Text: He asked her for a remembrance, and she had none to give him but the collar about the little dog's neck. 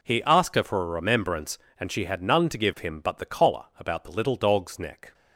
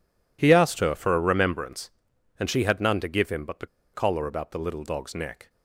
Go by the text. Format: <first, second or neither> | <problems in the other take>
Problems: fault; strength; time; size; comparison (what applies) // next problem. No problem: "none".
first | pauses between "the" and "collar"; slight; at 3.6 s; 0.27 s long